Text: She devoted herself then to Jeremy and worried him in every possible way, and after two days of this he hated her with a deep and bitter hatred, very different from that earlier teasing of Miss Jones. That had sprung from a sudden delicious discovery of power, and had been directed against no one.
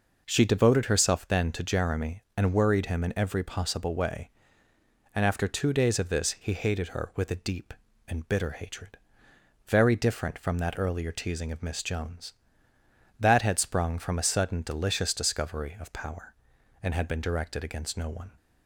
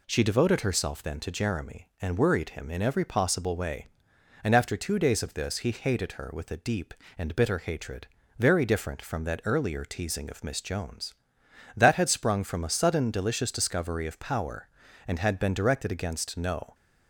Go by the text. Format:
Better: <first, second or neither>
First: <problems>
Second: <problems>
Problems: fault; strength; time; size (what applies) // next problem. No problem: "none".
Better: first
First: none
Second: stops before "one"; at 16.7 s